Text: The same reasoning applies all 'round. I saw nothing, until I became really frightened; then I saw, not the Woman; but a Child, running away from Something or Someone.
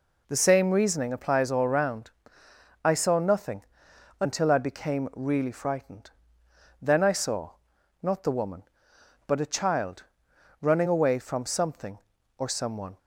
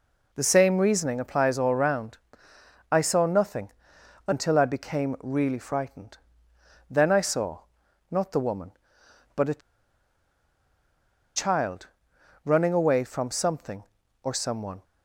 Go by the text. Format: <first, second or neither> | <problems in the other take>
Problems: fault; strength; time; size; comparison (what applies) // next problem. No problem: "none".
first | pauses between "a" and "Child"; strong; at 9.6 s; 1.7 s long